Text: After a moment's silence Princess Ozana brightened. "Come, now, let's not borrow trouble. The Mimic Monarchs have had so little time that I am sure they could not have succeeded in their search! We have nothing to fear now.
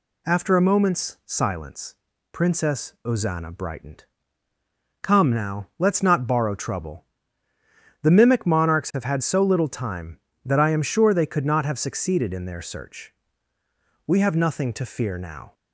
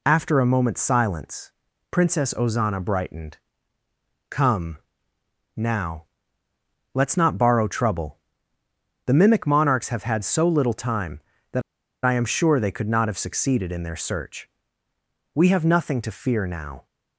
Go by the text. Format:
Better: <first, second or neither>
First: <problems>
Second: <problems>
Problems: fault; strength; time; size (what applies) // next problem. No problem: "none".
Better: first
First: pauses between "silence" and "Princess"; slight; at 1.9 s; 0.36 s long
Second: pauses between "silence" and "Princess"; at 1.5 s; 0.40 s long // pauses between "that" and "I"; at 11.6 s; 0.44 s long